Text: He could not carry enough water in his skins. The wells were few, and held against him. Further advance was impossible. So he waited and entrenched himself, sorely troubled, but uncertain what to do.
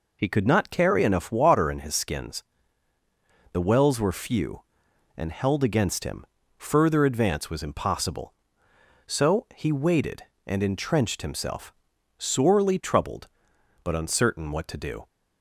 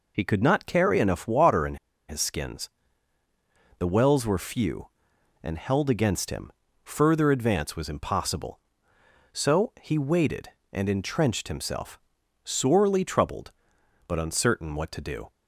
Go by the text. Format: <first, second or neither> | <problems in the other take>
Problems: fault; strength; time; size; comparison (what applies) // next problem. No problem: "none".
first | pauses between "in" and "his"; slight; at 1.7 s; 0.32 s long